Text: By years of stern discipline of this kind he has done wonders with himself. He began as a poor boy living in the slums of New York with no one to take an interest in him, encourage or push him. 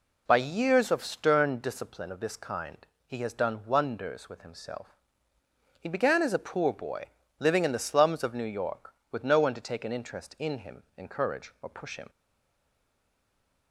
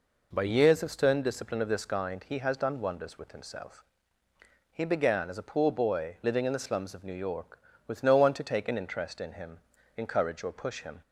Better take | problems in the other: second | pauses between "kind" and "he"; slight; at 2.8 s; 0.22 s long // pauses between "boy" and "living"; slight; at 7.0 s; 0.32 s long // stays silent after the last word; noticeable; from 12.0 s on; 1.7 s long

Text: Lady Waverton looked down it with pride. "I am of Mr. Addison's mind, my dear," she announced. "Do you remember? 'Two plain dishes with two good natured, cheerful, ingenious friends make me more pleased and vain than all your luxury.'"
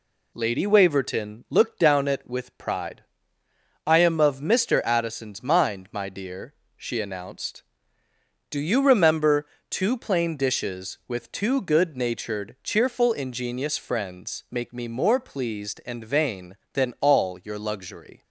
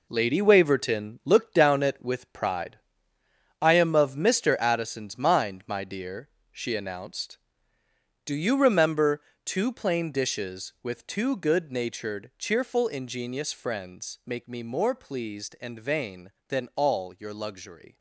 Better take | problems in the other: first | gets quieter; strong; throughout; 8.5 dB

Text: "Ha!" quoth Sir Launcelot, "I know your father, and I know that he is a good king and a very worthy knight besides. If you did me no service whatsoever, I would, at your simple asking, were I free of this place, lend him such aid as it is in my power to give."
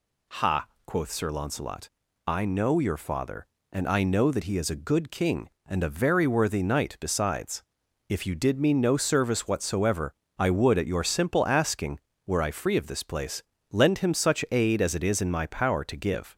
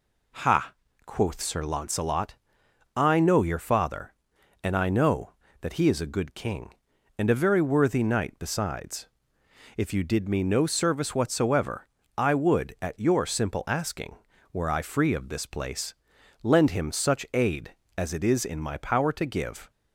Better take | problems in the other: neither | none

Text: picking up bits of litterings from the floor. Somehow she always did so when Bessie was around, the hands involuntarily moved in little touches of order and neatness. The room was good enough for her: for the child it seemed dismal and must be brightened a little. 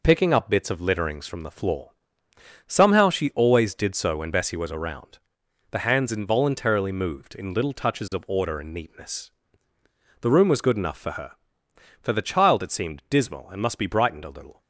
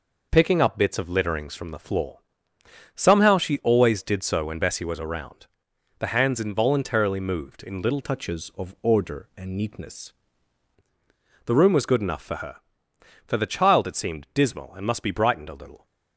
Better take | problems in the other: first | changes voice from "touches" to "neatness"; from 8.0 to 10.1 s; 2.1 s long

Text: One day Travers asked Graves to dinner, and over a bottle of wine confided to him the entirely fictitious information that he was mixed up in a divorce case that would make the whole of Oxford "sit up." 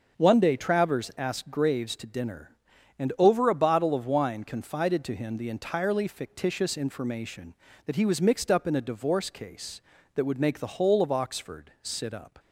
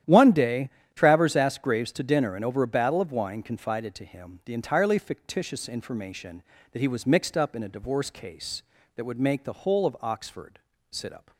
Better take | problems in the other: first | starts louder than the rest; strong; until 1.3 s; 11 dB; also in the first // pauses between "day" and "Travers"; slight; at 0.6 s; 0.26 s long // says "battle" for "bottle"; at 2.6 s // pauses between "Oxford" and "sit"; slight; at 10.5 s; 0.32 s long

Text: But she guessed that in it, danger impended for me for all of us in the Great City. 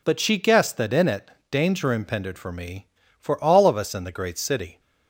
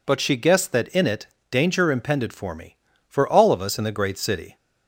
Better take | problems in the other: neither | none

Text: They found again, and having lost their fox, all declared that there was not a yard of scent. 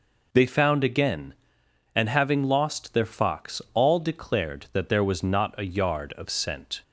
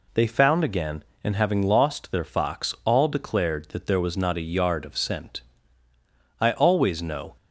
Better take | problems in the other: first | goes on to say "I always know"; noticeable; from 6.4 s on; 0.94 s long

